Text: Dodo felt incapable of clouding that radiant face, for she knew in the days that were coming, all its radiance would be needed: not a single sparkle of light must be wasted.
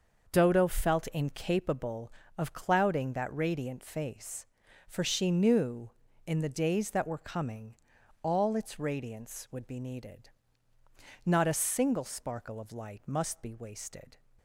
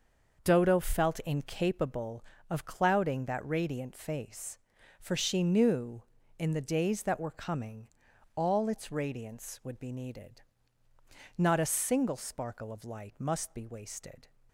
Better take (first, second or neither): neither